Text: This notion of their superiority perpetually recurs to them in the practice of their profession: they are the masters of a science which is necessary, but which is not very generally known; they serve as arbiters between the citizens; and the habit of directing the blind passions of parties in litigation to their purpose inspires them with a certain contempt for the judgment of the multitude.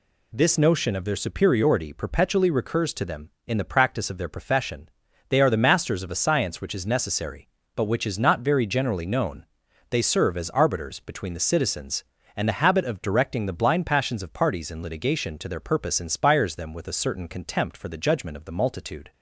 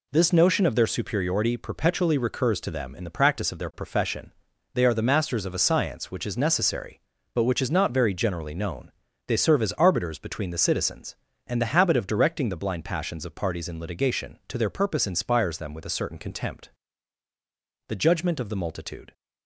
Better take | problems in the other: first | skips "for"; at 17.2 s

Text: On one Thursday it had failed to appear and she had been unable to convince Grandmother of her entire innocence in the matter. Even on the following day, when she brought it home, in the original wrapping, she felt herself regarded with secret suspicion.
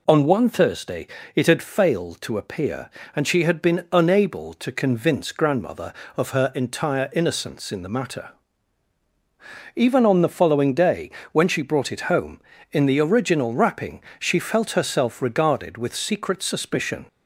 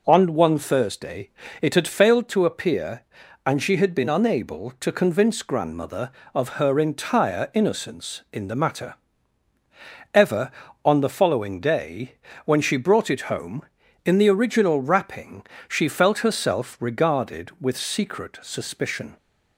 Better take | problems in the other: first | pauses between "Thursday" and "it"; slight; at 1.2 s; 0.32 s long; slight in the first // says "Ever" for "Even"; at 10.1 s

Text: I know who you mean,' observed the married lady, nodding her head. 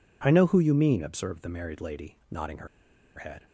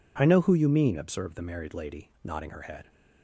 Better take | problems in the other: second | pauses between "her" and "head"; noticeable; at 2.6 s; 0.50 s long

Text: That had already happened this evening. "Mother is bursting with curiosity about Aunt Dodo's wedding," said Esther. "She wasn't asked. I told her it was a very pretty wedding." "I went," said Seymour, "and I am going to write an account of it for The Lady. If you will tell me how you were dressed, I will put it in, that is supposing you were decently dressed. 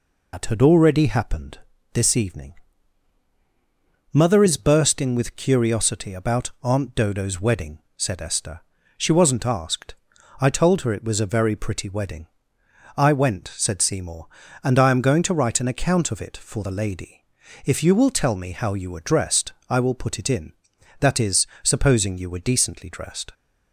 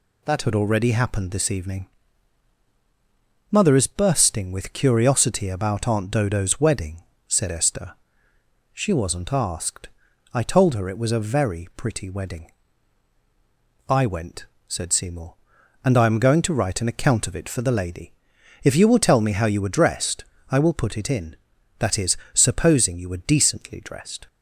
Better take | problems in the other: second | loses the start of "That"; at 0.3 s; 110 ms // pauses between "happened" and "this"; slight; at 1.5 s; 0.34 s long // pauses between "is" and "supposing"; slight; at 21.4 s; 0.16 s long; slight in the second

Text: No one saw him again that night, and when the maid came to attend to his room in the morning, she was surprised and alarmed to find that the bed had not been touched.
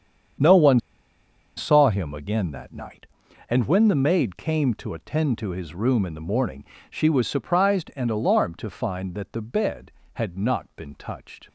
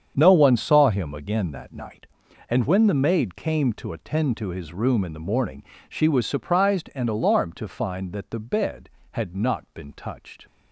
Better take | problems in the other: second | starts louder than the rest; strong; until 2.1 s; 8 dB; strong in the second // pauses between "one" and "saw"; noticeable; at 0.7 s; 0.77 s long

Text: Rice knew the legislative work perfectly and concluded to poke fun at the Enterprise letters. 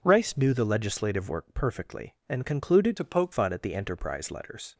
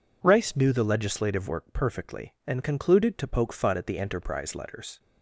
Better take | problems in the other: second | changes voice from "to" to "poke"; from 2.9 to 3.3 s; 0.4 s long

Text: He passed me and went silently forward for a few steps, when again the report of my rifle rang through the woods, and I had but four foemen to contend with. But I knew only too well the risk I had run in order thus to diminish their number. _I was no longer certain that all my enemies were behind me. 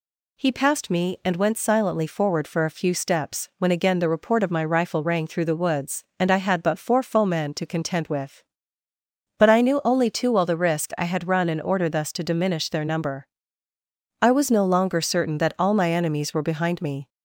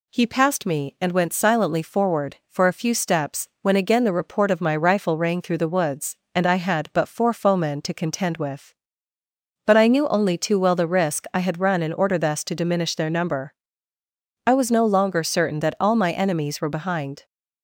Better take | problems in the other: first | stops before "me"; at 17.2 s

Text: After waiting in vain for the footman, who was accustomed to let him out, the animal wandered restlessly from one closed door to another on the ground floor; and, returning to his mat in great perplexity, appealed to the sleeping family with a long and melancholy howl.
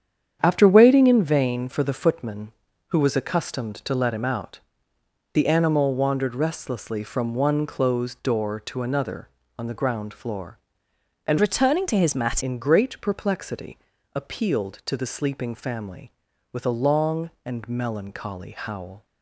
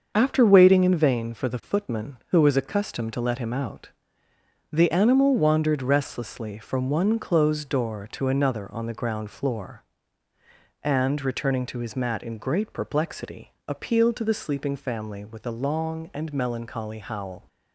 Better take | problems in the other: second | starts louder than the rest; strong; until 1.4 s; 8.5 dB; also in the second // changes voice from "returning" to "mat"; from 11.3 to 12.4 s; 1.1 s long

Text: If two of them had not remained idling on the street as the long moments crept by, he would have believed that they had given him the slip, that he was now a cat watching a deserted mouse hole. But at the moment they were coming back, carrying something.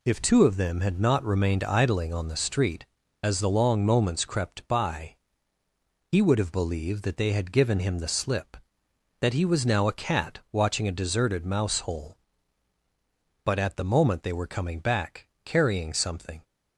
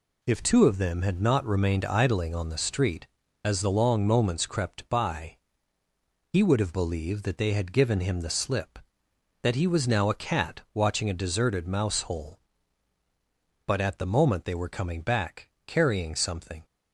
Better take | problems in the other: neither | none

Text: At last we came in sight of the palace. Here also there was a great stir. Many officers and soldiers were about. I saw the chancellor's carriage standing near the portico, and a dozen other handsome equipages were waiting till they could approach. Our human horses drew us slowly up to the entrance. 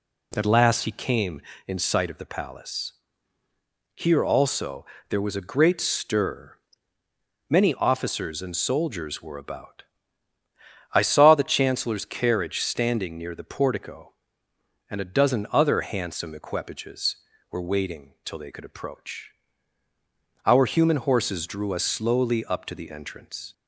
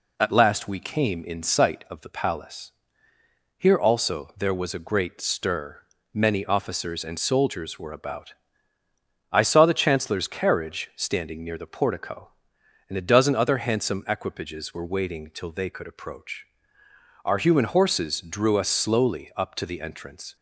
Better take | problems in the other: second | says "he" for "we"; at 0.8 s // pauses between "also" and "there"; slight; at 4.8 s; 0.24 s long

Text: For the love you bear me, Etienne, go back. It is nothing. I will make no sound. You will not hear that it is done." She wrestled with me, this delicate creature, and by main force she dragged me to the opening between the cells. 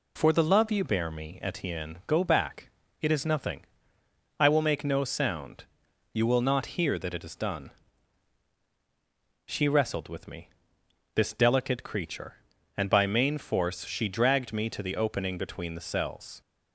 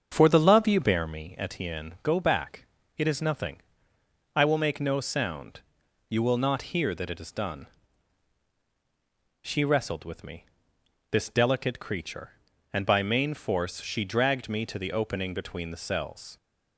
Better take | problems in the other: first | starts louder than the rest; strong; until 1.2 s; 7 dB

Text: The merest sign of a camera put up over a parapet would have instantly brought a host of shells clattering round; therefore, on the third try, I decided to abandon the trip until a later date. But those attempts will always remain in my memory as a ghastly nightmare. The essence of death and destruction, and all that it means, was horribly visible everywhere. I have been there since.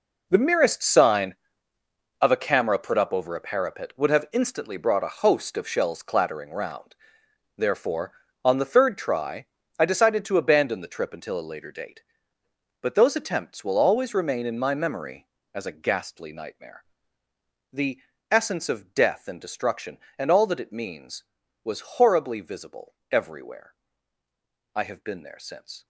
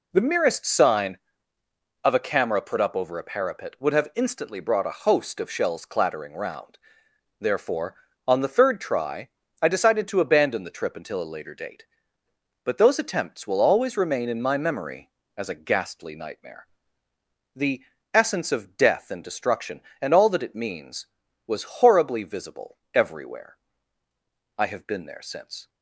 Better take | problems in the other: second | gets quieter; strong; throughout; 12.5 dB // pauses between "The" and "essence"; slight; at 17.9 s; 0.32 s long; slight in the second // pauses between "visible" and "everywhere"; slight; at 22.9 s; 0.16 s long; slight in the second

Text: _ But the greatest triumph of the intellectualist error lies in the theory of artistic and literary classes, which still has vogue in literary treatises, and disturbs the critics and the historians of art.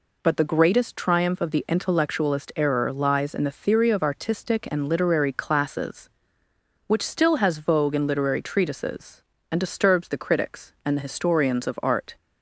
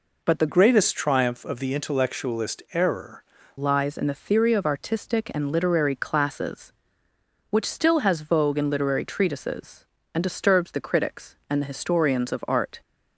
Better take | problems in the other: first | changes voice from "greatest" to "error"; from 0.4 to 3.2 s; 2.8 s long

